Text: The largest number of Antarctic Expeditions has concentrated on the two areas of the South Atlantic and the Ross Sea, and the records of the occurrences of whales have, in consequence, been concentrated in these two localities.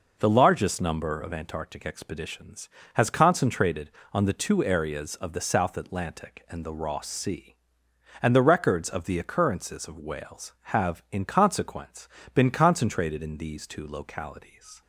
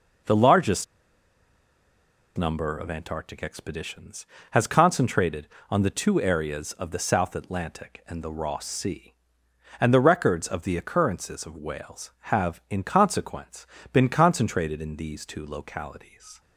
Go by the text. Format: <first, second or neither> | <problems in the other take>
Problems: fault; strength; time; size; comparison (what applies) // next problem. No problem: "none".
first | pauses between "largest" and "number"; strong; at 0.8 s; 1.5 s long